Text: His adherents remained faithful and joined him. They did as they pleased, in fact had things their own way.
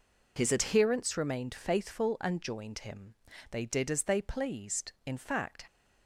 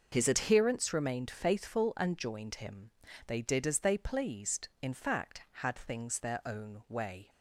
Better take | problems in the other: second | stops before "had things their own way"; at 5.6 s

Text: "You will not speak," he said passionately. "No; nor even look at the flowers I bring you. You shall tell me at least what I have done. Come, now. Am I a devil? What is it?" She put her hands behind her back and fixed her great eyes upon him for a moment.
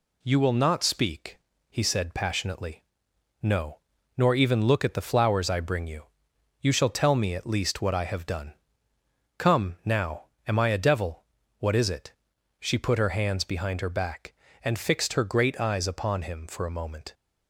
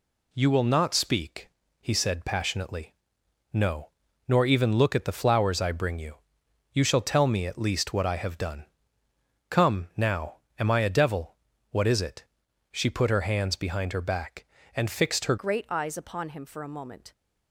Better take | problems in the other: first | changes voice at "great"; from 15.3 s on; 1.8 s long

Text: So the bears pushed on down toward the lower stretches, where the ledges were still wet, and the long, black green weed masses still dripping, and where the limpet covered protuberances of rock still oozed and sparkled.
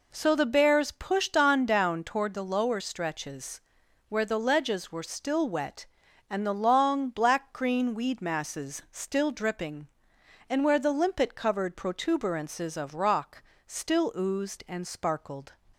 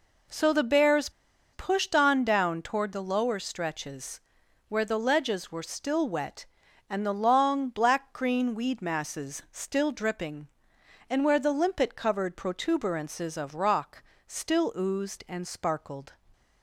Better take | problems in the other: first | pauses between "bears" and "pushed"; at 1.0 s; 0.43 s long // pauses between "rock" and "still"; slight; at 14.0 s; 0.24 s long; slight in the first

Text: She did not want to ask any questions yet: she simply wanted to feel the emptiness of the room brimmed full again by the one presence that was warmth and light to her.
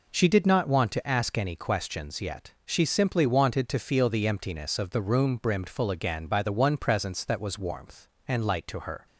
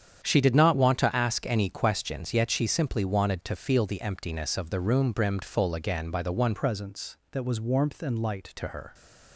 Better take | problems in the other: first | starts louder than the rest; strong; until 1.2 s; 8.5 dB // changes voice from "presence" to "light"; from 6.5 to 8.5 s; 2.0 s long

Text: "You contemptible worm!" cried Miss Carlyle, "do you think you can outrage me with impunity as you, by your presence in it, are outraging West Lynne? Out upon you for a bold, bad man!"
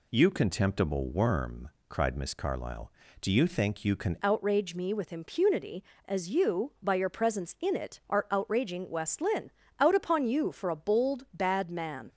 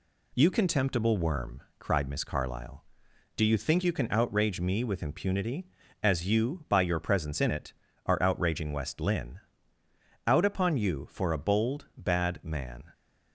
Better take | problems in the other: second | changes voice at "outrage"; from 4.2 s on; 7.8 s long

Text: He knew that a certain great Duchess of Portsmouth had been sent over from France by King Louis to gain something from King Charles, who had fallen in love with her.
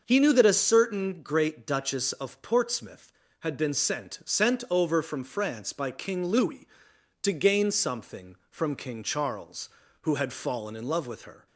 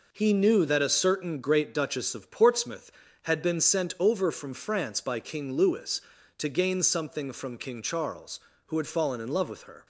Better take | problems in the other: second | starts louder than the rest; until 1.0 s; 6.5 dB // says "sent" twice; at 4.2 s

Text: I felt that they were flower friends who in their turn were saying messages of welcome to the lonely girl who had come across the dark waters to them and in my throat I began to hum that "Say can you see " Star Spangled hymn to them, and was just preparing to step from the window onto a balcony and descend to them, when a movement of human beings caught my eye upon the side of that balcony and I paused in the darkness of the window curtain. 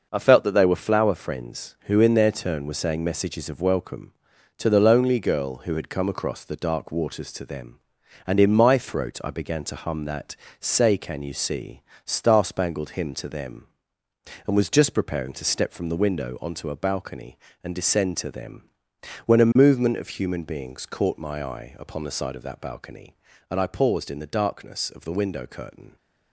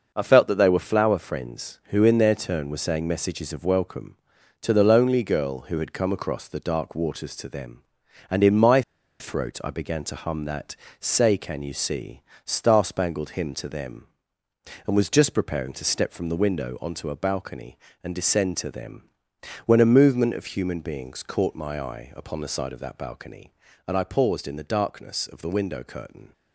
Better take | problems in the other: first | pauses between "my" and "throat"; at 8.8 s; 0.37 s long // pauses between "that" and "Say"; slight; at 10.7 s; 0.26 s long; slight in the first

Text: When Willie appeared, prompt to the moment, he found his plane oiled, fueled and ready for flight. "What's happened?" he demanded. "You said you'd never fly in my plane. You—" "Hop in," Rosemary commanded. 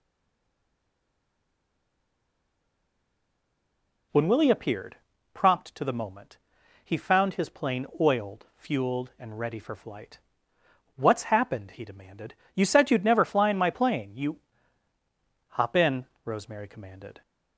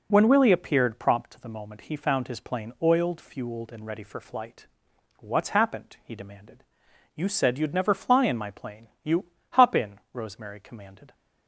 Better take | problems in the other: second | stays silent before the first word; strong; until 4.1 s; 4.1 s long

